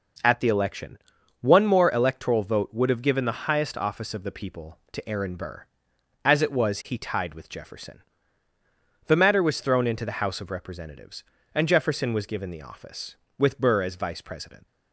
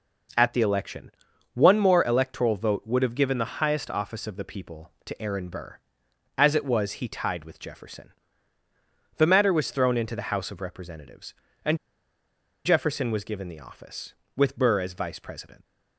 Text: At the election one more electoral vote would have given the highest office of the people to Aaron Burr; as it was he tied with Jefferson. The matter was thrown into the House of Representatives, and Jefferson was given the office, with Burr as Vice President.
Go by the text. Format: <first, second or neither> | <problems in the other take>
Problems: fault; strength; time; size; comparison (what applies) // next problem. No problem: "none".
first | pauses between "election" and "one"; at 1.1 s; 0.44 s long; also in the first // pauses between "and" and "Jefferson"; noticeable; at 11.7 s; 0.88 s long